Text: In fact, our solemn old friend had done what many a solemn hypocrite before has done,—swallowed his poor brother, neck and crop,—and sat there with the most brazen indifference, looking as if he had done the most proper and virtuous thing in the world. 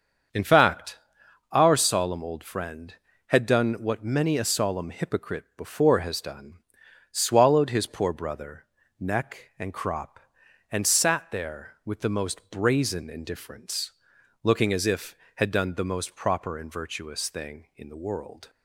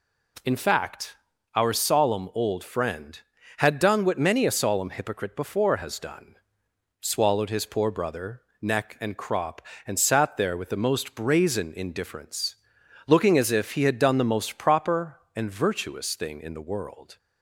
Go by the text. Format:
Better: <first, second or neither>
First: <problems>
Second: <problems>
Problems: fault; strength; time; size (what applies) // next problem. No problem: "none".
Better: second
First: starts louder than the rest; strong; until 1.8 s; 7.5 dB // skips "he"; at 15.2 s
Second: none